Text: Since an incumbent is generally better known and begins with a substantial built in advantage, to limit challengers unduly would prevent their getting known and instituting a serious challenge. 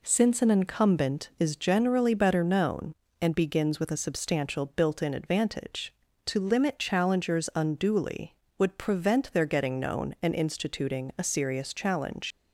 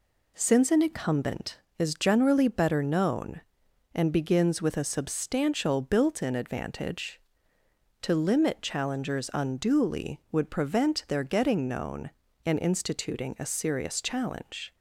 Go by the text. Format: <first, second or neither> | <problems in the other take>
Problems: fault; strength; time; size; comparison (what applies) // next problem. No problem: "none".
second | leaves "challenge" unfinished; at 12.3 s; 110 ms